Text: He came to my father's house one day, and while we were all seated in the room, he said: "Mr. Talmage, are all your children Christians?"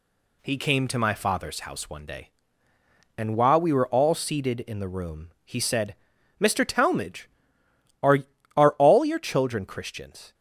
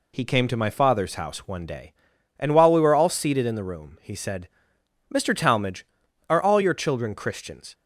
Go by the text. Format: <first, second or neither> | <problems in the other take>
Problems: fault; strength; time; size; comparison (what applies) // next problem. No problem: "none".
second | says "are" twice; at 8.5 s